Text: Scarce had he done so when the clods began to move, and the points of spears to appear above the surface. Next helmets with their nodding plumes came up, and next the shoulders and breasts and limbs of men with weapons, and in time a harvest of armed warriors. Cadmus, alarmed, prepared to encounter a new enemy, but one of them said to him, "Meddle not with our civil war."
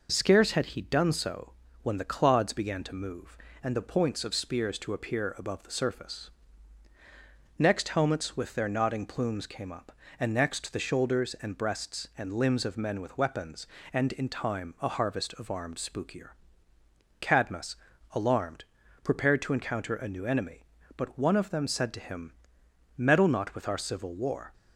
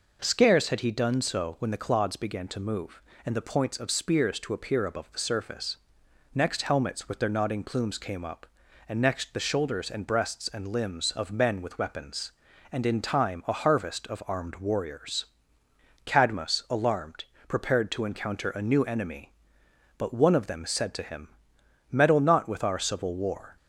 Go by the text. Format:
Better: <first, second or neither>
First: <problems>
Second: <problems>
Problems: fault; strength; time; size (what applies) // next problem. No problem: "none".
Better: second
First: pauses between "so" and "when"; slight; at 1.5 s; 0.30 s long // says "spookier" for "warriors"; at 15.7 s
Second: none